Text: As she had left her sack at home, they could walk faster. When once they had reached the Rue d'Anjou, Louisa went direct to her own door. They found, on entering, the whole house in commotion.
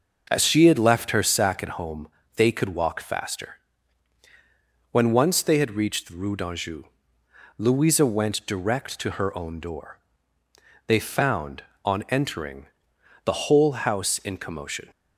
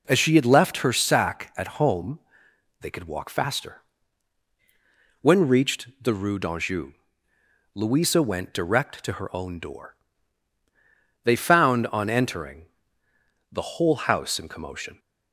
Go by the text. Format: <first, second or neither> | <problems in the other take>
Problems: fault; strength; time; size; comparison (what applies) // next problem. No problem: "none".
first | skips "once they had"; at 5.4 s